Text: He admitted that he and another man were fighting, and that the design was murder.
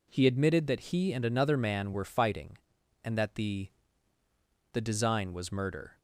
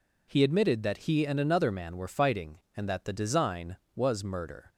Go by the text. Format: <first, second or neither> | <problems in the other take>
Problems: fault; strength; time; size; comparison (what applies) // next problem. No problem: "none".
second | says "the" twice; at 4.7 s